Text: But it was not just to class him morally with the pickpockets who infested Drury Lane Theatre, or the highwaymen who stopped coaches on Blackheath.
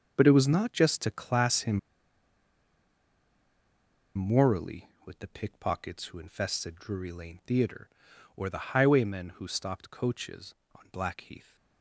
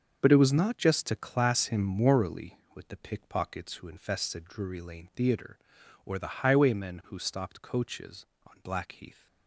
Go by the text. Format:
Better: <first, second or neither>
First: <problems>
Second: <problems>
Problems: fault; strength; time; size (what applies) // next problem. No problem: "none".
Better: second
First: starts louder than the rest; until 1.1 s; 6.5 dB // pauses between "him" and "morally"; strong; at 1.7 s; 2.3 s long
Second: starts louder than the rest; until 1.2 s; 6.5 dB